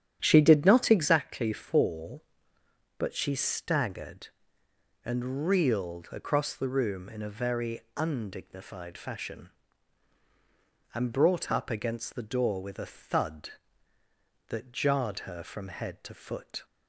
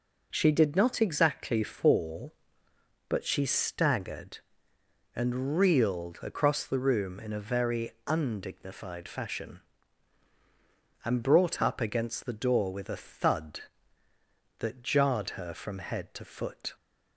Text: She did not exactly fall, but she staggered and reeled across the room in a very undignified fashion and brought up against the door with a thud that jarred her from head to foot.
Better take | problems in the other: second | starts louder than the rest; strong; until 1.2 s; 9.5 dB // pauses between "very" and "undignified"; slight; at 7.8 s; 0.16 s long; slight in the second

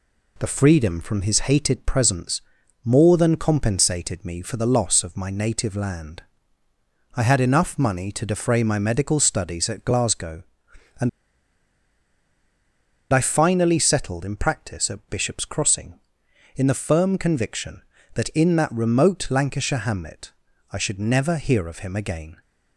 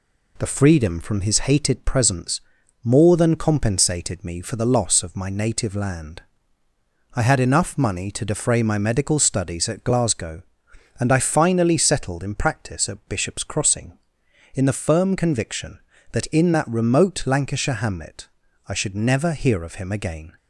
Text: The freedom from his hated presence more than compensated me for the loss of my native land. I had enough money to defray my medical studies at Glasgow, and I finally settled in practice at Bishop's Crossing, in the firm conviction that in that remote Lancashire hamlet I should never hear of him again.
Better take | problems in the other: second | pauses between "presence" and "more"; at 2.4 s; 0.44 s long; also in the second // pauses between "and" and "I"; strong; at 11.0 s; 2.0 s long // pauses between "hamlet" and "I"; at 20.3 s; 0.40 s long; also in the second

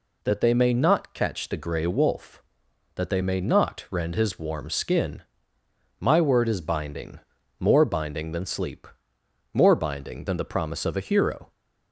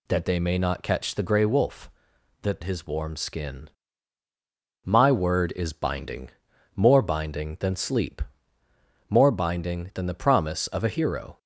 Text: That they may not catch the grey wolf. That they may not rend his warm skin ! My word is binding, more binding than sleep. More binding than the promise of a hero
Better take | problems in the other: first | skips "they may not rend"; at 2.6 s

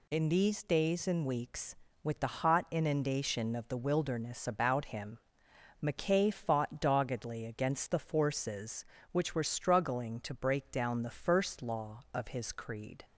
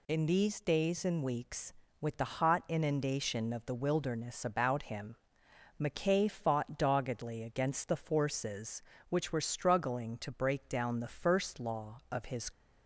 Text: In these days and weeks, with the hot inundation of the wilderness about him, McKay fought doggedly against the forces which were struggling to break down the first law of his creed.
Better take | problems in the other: first | stops before "creed"; at 12.5 s

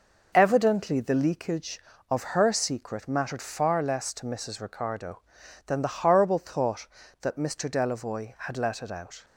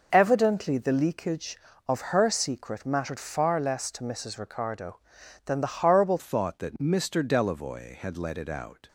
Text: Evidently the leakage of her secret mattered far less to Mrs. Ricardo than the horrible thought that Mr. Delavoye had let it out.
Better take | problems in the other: first | changes voice at "thought"; from 6.1 s on; 2.7 s long

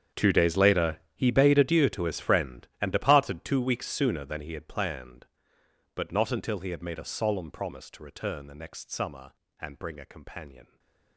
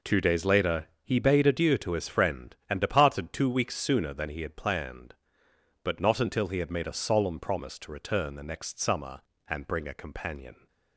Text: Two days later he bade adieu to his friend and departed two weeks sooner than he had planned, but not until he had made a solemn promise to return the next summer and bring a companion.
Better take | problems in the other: second | gets quieter; strong; throughout; 18.5 dB // pauses between "later" and "he"; slight; at 0.9 s; 0.16 s long; slight in the second // stays silent after the last word; slight; from 10.6 s on; 0.5 s long

